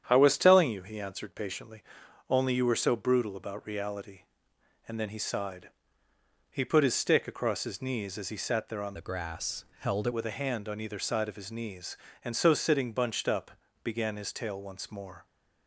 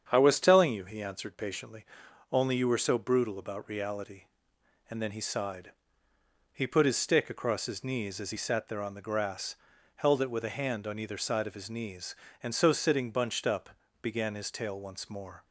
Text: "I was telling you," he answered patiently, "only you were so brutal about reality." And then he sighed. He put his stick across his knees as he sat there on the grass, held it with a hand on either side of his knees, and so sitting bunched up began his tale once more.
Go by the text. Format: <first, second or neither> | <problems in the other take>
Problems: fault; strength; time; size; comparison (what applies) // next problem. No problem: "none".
second | starts louder than the rest; strong; until 1.0 s; 9 dB; strong in the second // changes voice from "the" to "it"; from 8.9 to 10.1 s; 1.2 s long // pauses between "up" and "began"; slight; at 13.5 s; 0.32 s long; slight in the second